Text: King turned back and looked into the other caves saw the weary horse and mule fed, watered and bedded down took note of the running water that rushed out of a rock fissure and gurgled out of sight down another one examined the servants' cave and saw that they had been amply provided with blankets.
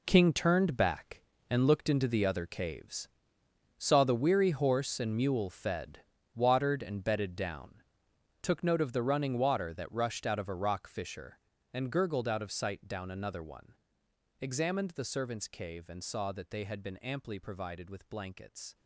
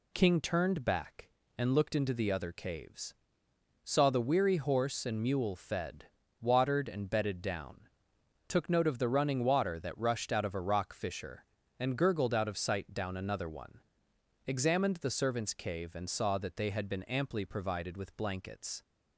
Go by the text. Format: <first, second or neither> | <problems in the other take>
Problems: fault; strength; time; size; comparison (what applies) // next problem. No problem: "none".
second | gets quieter; strong; throughout; 12.5 dB // pauses between "caves" and "saw"; noticeable; at 3.0 s; 0.68 s long; noticeable in the second // pauses between "down" and "took"; noticeable; at 7.8 s; 0.60 s long; noticeable in the second // pauses between "one" and "examined"; noticeable; at 13.7 s; 0.66 s long; noticeable in the second